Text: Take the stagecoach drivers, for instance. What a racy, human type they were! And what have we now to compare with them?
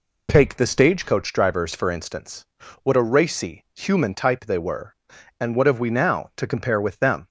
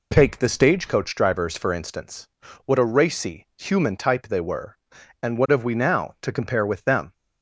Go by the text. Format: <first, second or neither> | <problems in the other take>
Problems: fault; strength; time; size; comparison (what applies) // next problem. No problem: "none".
neither | none